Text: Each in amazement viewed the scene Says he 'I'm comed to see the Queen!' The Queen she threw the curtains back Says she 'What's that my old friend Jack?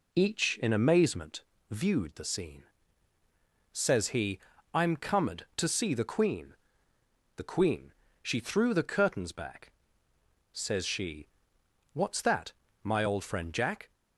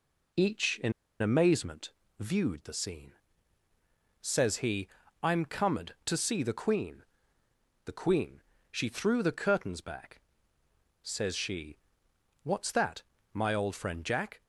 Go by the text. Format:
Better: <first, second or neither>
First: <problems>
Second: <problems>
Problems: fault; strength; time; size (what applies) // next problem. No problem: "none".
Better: first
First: pauses between "amazement" and "viewed"; slight; at 1.4 s; 0.28 s long // pauses between "scene" and "Says"; at 2.6 s; 1.0 s long // pauses between "he" and "I'm"; slight; at 4.3 s; 0.34 s long // pauses between "Queen" and "she"; slight; at 7.9 s; 0.28 s long // pauses between "back" and "Says"; noticeable; at 9.7 s; 0.80 s long // pauses between "she" and "What's"; noticeable; at 11.2 s; 0.64 s long // pauses between "that" and "my"; slight; at 12.5 s; 0.32 s long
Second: pauses between "in" and "amazement"; slight; at 0.9 s; 0.30 s long // pauses between "amazement" and "viewed"; slight; at 1.9 s; 0.28 s long // pauses between "scene" and "Says"; at 3.1 s; 1.0 s long // pauses between "he" and "I'm"; slight; at 4.8 s; 0.34 s long // pauses between "Queen" and "she"; slight; at 8.4 s; 0.28 s long // pauses between "back" and "Says"; noticeable; at 10.2 s; 0.82 s long // pauses between "she" and "What's"; noticeable; at 11.7 s; 0.64 s long // pauses between "that" and "my"; slight; at 13.0 s; 0.32 s long